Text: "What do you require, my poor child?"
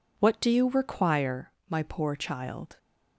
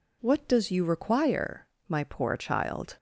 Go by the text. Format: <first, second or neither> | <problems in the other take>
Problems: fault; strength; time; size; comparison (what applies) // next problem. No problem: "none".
first | says "does" for "do"; at 0.4 s